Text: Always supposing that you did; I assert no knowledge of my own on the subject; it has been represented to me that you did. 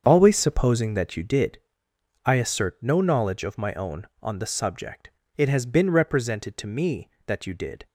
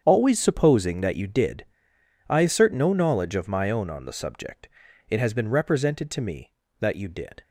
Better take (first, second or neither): neither